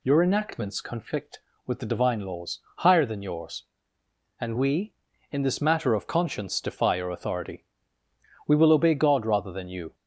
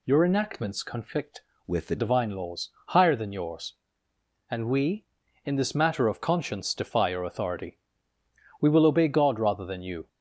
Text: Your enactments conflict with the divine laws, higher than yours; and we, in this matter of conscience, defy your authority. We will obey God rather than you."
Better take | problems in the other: first | changes voice from "with" to "the"; from 1.6 to 1.9 s; 0.3 s long

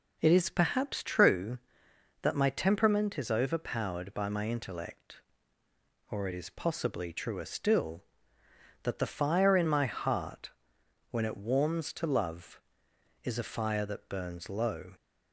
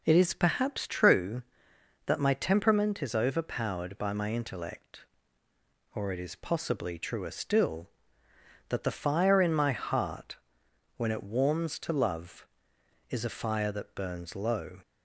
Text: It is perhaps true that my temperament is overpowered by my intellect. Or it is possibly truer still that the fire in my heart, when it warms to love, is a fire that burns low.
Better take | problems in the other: neither | none

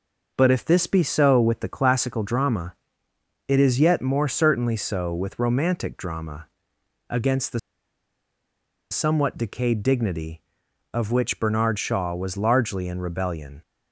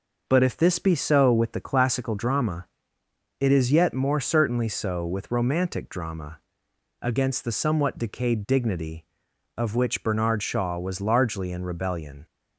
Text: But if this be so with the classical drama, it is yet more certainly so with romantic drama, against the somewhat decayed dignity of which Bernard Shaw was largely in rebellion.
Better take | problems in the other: second | pauses between "the" and "somewhat"; strong; at 7.5 s; 1.3 s long

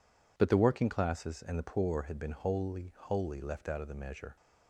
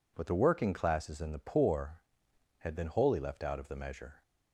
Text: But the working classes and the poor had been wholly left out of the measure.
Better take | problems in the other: second | says "wholly" twice; at 2.9 s

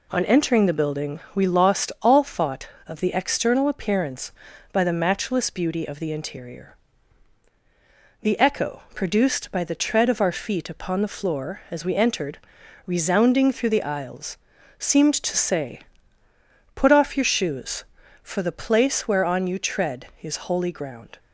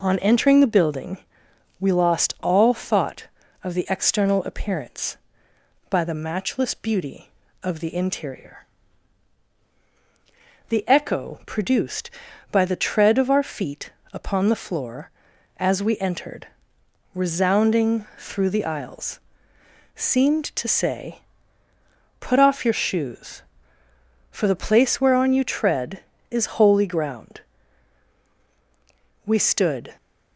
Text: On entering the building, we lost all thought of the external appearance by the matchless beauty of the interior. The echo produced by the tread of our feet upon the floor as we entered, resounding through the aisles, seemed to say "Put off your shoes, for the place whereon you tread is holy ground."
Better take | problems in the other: first | pauses between "feet" and "upon"; slight; at 13.9 s; 0.20 s long // pauses between "say" and "Put"; at 21.1 s; 1.0 s long; noticeable in the first // goes on to say "We stood"; noticeable; from 29.2 s on; 0.70 s long

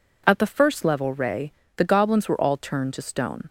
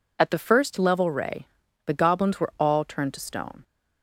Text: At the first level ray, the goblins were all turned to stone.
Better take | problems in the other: neither | none

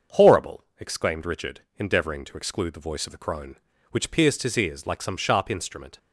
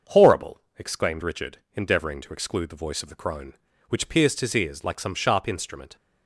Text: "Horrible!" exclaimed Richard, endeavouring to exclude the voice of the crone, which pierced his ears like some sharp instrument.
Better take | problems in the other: neither | starts louder than the rest; the same in both

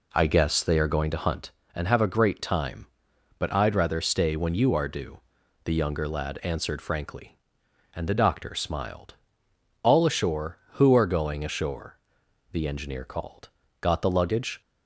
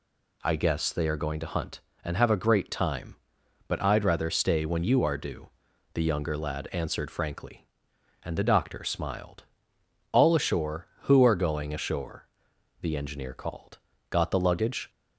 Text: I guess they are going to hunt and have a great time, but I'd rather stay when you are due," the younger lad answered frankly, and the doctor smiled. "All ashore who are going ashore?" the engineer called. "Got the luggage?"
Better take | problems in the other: second | starts louder than the rest; slight; until 1.5 s; 3 dB

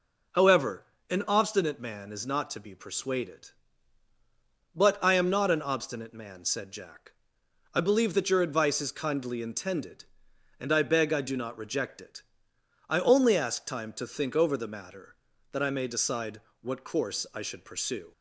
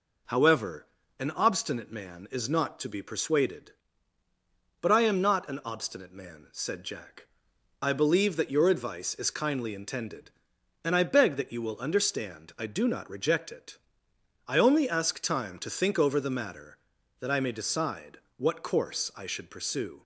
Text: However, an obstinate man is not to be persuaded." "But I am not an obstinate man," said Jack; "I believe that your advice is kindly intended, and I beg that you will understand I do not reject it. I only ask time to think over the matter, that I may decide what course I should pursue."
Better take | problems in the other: second | skips "that you will understand"; at 11.1 s // pauses between "decide" and "what"; slight; at 16.4 s; 0.22 s long; slight in the second

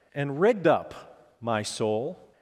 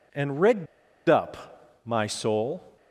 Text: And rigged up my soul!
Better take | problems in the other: first | pauses between "rigged" and "up"; at 0.6 s; 0.42 s long

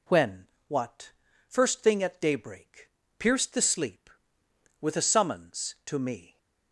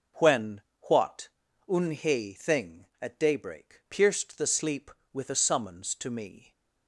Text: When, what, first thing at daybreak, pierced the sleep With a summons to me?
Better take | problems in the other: first | says "unhe" for "first"; at 1.6 s

